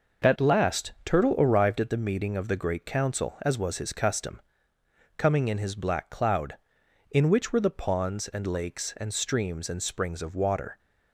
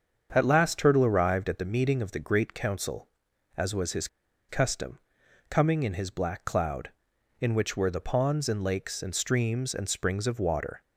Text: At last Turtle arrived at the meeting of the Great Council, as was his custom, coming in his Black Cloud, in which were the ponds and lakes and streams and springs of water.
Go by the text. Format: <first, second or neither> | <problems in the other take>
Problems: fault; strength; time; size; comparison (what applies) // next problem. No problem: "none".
first | starts louder than the rest; strong; until 1.3 s; 7 dB // pauses between "his" and "custom"; at 4.0 s; 0.41 s long